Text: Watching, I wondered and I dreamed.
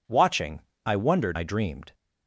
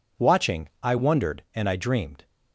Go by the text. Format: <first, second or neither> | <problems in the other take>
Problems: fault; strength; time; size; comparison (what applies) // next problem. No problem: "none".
second | skips "and"; at 1.3 s